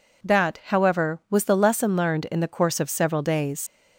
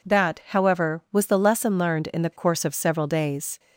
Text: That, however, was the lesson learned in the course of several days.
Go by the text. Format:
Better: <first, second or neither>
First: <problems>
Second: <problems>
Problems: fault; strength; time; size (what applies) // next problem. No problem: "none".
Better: second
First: leaves "days" unfinished; at 3.6 s; 75 ms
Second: none